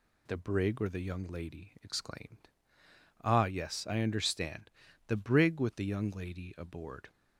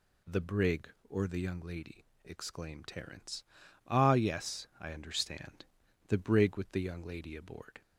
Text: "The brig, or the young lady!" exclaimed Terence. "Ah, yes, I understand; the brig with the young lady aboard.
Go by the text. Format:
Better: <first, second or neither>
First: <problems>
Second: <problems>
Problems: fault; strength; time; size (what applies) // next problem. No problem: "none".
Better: second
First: skips "Terence"; at 2.8 s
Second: none